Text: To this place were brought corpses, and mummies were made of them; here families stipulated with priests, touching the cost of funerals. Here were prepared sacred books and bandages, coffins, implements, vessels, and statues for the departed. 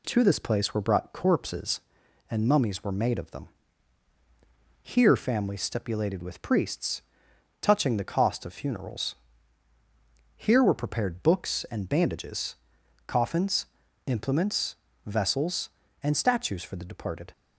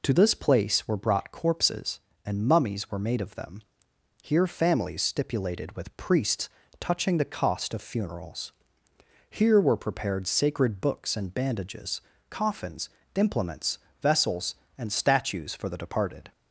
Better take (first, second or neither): second